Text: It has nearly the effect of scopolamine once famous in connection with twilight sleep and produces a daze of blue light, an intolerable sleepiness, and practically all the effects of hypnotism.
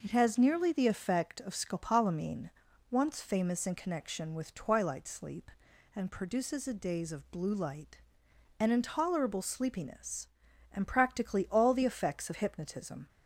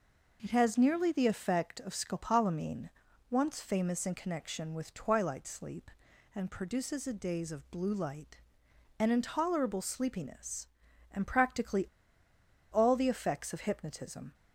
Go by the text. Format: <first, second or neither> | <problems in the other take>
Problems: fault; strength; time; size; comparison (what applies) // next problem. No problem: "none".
first | pauses between "scopolamine" and "once"; at 2.8 s; 0.40 s long; also in the first // pauses between "practically" and "all"; noticeable; at 11.8 s; 0.88 s long